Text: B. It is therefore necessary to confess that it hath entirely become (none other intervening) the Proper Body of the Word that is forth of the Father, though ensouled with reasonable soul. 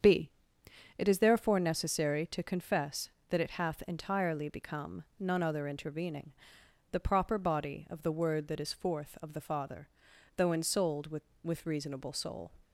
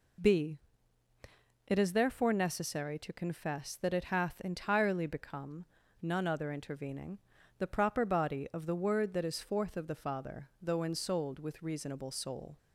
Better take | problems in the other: second | starts louder than the rest; strong; until 1.6 s; 7.5 dB // says "with" twice; at 11.4 s

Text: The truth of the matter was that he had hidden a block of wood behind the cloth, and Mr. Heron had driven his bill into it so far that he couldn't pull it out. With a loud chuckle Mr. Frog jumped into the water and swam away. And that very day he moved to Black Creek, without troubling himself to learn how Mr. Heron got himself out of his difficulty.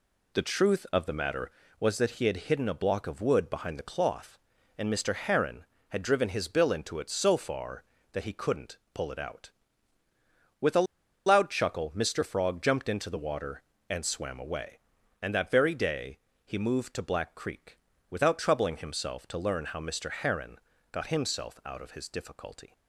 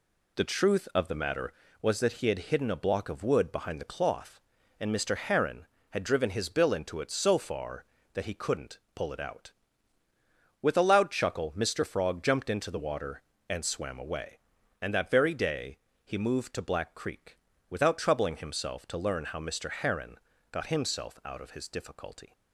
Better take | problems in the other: second | pauses between "couldn't" and "pull"; slight; at 8.7 s; 0.16 s long; slight in the second // pauses between "a" and "loud"; at 10.8 s; 0.40 s long // pauses between "day" and "he"; slight; at 16.1 s; 0.26 s long; slight in the second // pauses between "Heron" and "got"; slight; at 20.5 s; 0.34 s long; slight in the second

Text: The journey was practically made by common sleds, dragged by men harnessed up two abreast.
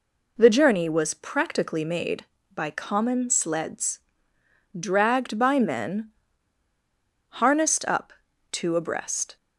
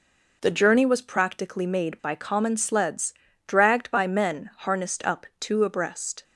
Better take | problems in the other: second | pauses between "men" and "harnessed"; at 6.1 s; 1.1 s long // pauses between "up" and "two"; at 8.1 s; 0.38 s long

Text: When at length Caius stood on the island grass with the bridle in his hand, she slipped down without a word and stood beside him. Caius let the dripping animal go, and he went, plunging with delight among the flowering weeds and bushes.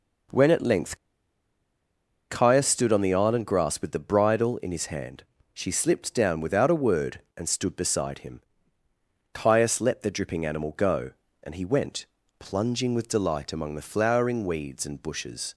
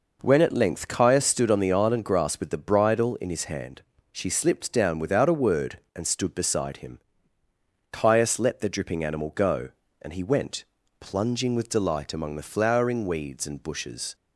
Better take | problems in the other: second | pauses between "length" and "Caius"; strong; at 0.9 s; 1.3 s long

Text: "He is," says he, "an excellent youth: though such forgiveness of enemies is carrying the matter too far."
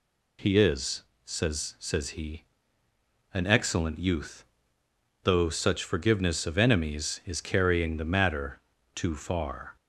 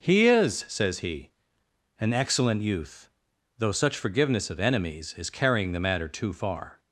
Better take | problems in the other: second | says "says" twice; at 1.7 s // pauses between "matter" and "too"; slight; at 8.6 s; 0.32 s long

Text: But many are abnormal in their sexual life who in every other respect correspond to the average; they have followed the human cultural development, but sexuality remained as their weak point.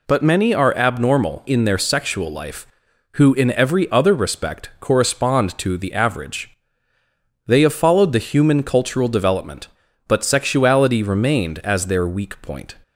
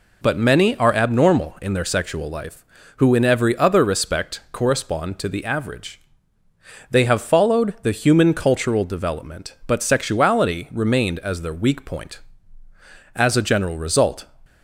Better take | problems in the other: first | goes on to say "As a general result"; noticeable; from 13.1 s on; 1.1 s long

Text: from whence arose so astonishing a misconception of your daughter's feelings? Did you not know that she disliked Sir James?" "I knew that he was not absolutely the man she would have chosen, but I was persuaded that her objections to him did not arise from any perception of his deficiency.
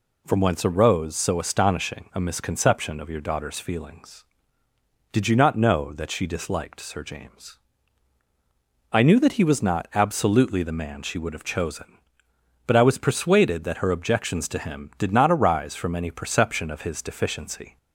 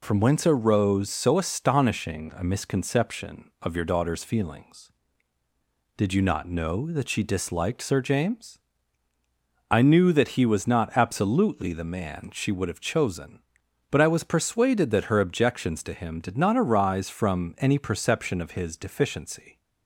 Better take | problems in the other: neither | none

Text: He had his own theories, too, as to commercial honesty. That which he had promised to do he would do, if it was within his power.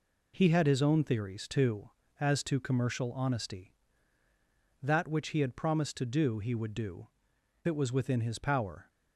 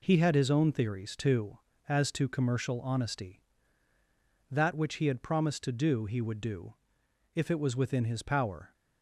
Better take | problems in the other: second | skips "if"; at 7.3 s

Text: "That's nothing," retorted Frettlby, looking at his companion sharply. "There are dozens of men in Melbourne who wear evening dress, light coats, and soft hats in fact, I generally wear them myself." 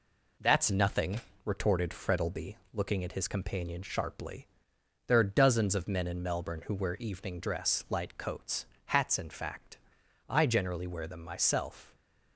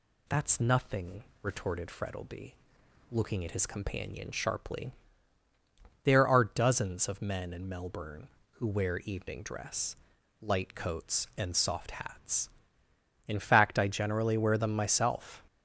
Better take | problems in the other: second | skips "and soft"; at 8.7 s

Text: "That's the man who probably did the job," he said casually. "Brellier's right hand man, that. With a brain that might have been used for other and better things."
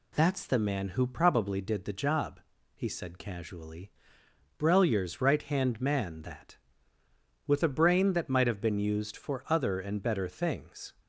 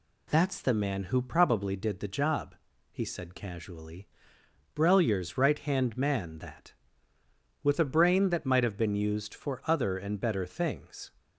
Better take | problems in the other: neither | none

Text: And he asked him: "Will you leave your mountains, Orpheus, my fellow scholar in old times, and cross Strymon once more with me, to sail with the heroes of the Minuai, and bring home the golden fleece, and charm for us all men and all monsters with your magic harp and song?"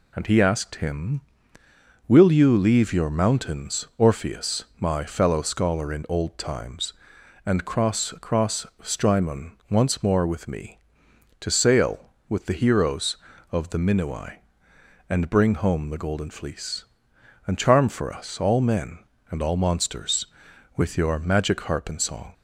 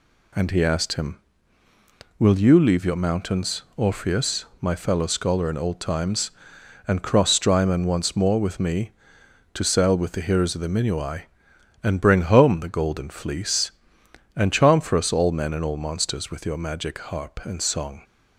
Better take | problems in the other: second | says "cross" twice; at 8.2 s // pauses between "Strymon" and "once"; slight; at 9.5 s; 0.16 s long

